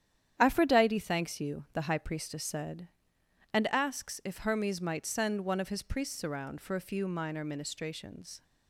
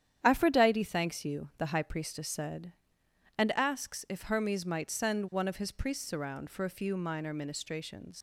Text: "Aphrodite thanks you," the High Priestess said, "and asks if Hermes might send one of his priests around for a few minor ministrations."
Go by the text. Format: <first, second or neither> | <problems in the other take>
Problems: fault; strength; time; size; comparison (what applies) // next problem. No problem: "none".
first | starts louder than the rest; strong; until 1.2 s; 9.5 dB; strong in the first // leaves "ministrations" unfinished; at 8.1 s; 110 ms